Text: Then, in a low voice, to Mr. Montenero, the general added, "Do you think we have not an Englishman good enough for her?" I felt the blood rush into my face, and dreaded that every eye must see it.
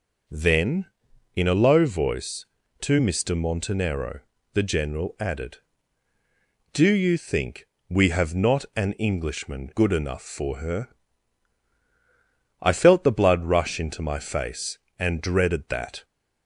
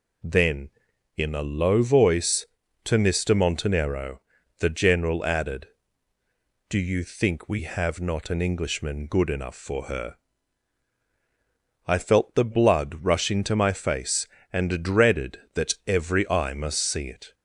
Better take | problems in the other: second | pauses between "think" and "we"; slight; at 7.6 s; 0.24 s long // stops before "every eye must see it"; at 16.0 s

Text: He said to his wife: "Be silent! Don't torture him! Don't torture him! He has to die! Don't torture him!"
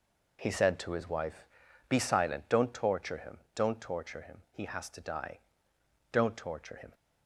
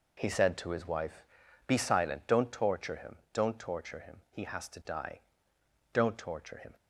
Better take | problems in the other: neither | none

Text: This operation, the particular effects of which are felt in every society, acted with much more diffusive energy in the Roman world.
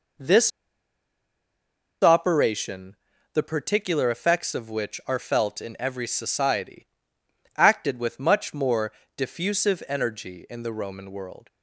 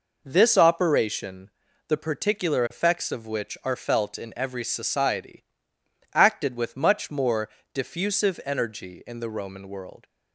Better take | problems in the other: second | pauses between "This" and "operation"; strong; at 0.5 s; 1.5 s long // pauses between "more" and "diffusive"; slight; at 8.9 s; 0.28 s long; slight in the second

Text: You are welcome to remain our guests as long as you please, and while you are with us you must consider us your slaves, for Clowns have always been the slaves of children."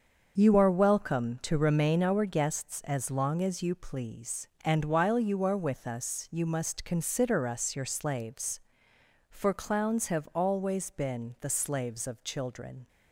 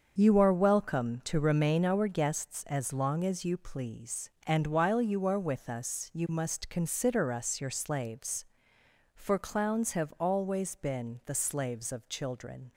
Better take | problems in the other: neither | starts louder than the rest; the same in both

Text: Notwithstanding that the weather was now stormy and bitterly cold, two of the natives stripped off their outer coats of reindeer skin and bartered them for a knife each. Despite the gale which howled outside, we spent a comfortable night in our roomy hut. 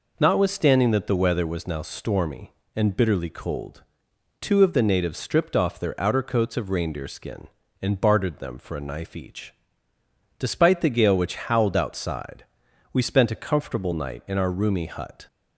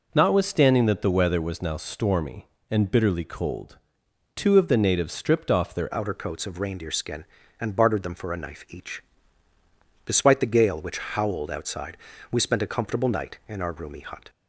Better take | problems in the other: first | changes voice at "outer"; from 5.9 s on; 8.3 s long

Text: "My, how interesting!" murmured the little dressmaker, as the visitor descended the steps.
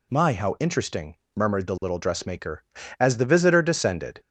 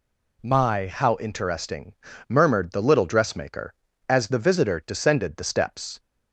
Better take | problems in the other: second | stops before "the steps"; at 4.2 s

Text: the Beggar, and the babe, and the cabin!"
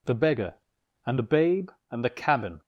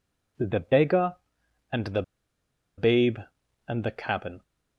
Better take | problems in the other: first | pauses between "the" and "babe"; noticeable; at 2.0 s; 0.74 s long

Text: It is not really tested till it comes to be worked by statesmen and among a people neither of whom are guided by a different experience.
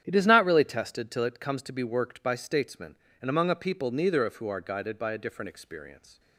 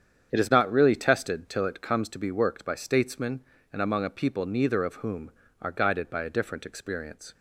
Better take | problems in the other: second | starts louder than the rest; strong; until 1.0 s; 9 dB; strong in the second // says "who" for "whom"; at 4.3 s

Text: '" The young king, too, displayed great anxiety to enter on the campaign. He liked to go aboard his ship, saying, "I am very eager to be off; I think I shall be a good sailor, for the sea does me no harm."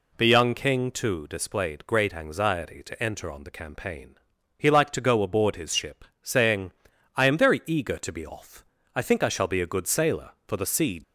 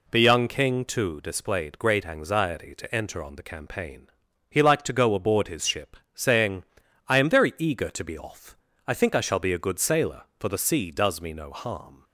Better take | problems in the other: second | stops before "does me no harm"; at 11.0 s

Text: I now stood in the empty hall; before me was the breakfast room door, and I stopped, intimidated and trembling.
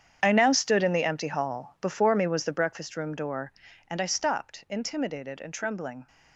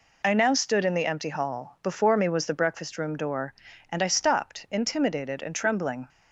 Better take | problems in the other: second | gets quieter; strong; throughout; 14.5 dB

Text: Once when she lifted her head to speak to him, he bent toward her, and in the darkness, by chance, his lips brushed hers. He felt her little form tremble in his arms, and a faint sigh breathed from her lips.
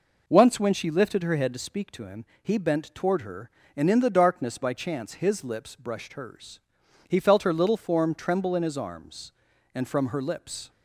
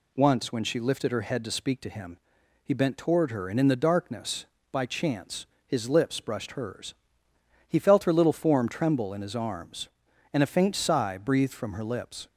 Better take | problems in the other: second | skips "a faint sigh breathed"; at 9.8 s

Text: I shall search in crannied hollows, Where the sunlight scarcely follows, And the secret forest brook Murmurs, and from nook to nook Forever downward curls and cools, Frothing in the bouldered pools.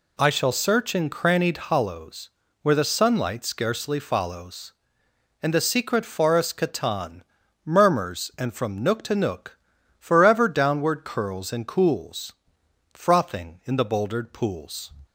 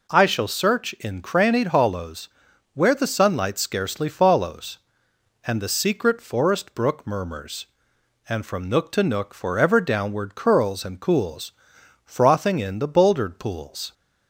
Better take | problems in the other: second | says "catan" for "brook"; at 6.5 s // pauses between "nook" and "Forever"; at 9.5 s; 0.40 s long

